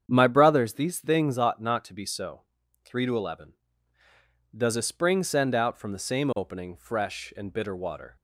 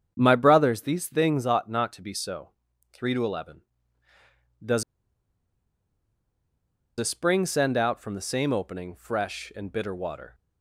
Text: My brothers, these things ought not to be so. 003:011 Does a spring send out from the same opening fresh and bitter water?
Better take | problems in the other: first | starts louder than the rest; strong; until 1.1 s; 8 dB; strong in the first // pauses between "Does" and "a"; strong; at 4.8 s; 2.1 s long

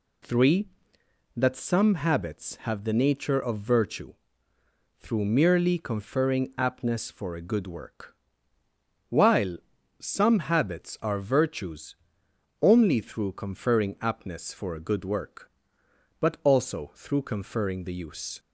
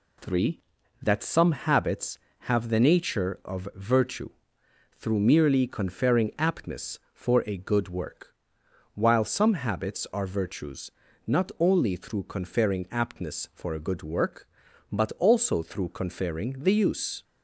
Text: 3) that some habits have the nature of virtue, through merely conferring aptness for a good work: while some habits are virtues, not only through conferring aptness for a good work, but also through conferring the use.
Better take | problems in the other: second | pauses between "while" and "some"; at 9.5 s; 0.42 s long // skips "not"; at 12.2 s

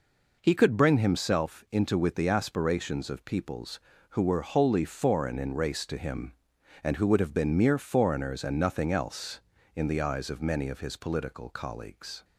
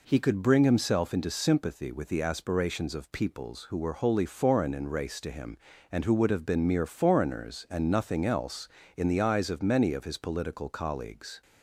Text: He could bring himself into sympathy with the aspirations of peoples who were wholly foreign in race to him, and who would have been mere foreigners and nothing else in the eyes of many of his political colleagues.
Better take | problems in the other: second | skips "sympathy"; at 1.9 s

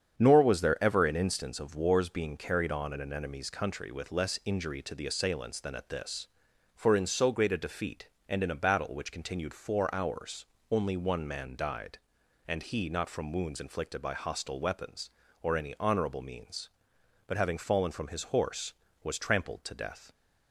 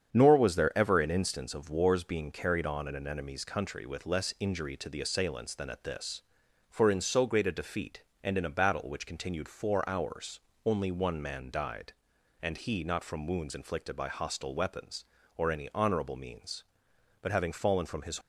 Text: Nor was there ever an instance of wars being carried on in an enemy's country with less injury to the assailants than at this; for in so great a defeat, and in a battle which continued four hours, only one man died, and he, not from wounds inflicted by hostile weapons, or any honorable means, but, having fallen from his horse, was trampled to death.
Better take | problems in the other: first | starts louder than the rest; strong; until 1.1 s; 8 dB; strong in the first // stops before "horse was trampled to death"; at 18.2 s

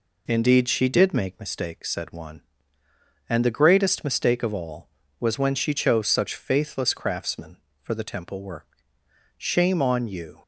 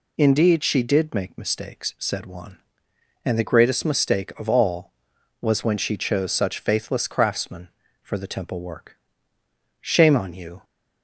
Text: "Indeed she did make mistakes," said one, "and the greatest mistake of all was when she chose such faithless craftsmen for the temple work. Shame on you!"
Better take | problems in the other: neither | none

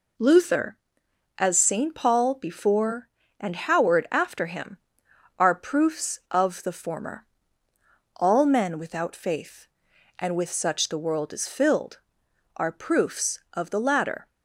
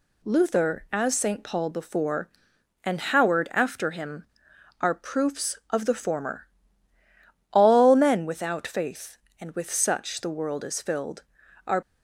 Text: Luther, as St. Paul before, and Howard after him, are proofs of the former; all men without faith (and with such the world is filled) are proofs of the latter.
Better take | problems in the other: first | stops before "proofs of the latter"; at 11.8 s

